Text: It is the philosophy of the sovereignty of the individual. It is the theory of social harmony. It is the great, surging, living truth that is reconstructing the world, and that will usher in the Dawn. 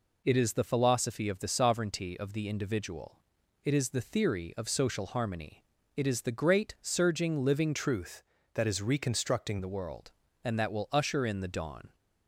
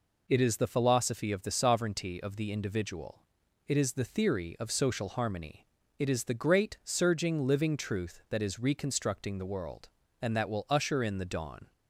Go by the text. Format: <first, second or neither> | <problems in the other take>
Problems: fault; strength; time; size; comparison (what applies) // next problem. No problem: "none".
second | changes voice from "truth" to "reconstructing"; from 7.7 to 9.5 s; 1.8 s long